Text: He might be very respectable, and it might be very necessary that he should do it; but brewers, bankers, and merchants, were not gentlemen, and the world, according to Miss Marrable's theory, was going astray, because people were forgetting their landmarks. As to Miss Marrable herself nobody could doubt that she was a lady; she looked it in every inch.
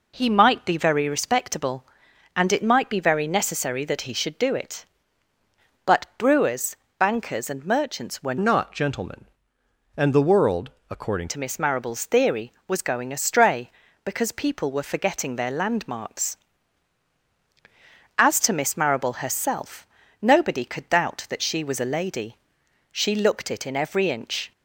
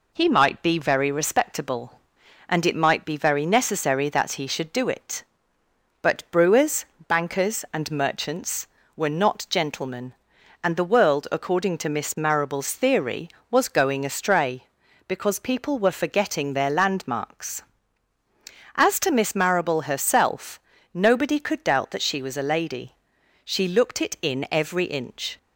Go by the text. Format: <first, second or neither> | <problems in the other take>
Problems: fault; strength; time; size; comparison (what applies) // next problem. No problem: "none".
second | changes voice from "not" to "according"; from 8.3 to 11.2 s; 2.9 s long // pauses between "herself" and "nobody"; slight; at 19.8 s; 0.34 s long; slight in the second